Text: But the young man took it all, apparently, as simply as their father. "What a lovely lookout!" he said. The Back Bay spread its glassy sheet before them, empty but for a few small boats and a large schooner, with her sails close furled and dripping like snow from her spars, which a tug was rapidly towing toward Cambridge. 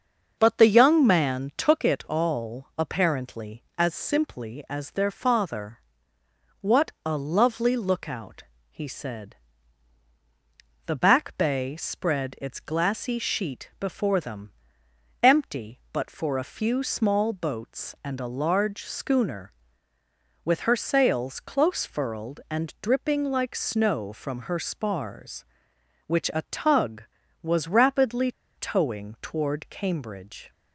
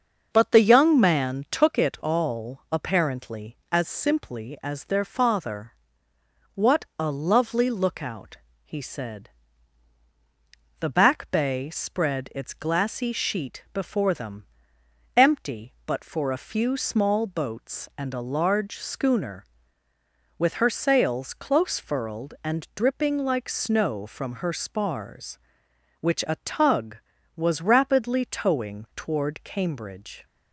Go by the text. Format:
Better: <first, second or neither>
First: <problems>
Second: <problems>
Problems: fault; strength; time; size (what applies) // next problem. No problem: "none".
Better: second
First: starts louder than the rest; until 1.4 s; 6 dB // pauses between "rapidly" and "towing"; slight; at 28.3 s; 0.25 s long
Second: starts louder than the rest; until 1.3 s; 6 dB